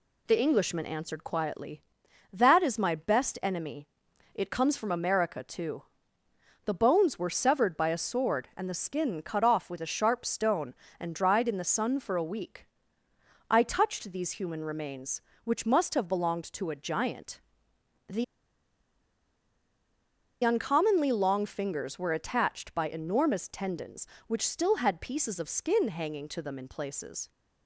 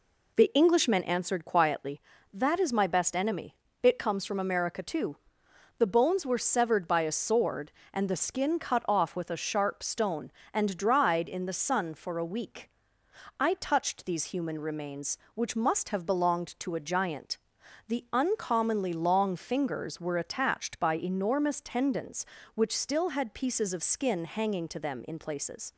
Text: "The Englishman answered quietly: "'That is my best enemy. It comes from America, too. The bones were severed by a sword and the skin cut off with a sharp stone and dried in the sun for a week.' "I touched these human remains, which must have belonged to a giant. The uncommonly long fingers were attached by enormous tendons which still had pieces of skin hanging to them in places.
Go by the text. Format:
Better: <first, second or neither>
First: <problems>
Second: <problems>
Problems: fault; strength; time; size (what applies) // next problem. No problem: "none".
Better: second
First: pauses between "The" and "uncommonly"; strong; at 18.2 s; 2.1 s long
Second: none